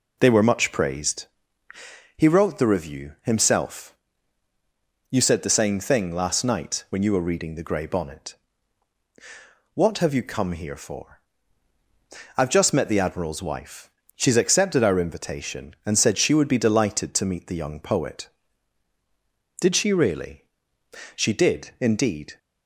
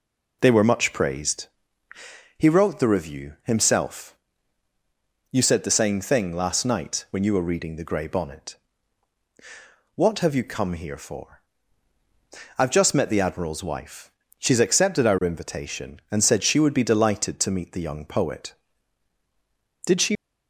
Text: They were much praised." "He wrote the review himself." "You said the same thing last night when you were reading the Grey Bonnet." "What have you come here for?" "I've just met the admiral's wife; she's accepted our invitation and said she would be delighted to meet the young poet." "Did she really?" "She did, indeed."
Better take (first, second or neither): first